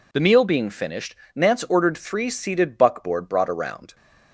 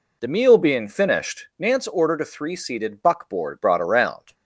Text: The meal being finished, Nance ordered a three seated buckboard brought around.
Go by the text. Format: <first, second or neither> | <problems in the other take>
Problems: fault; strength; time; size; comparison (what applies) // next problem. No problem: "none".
second | skips "a"; at 1.9 s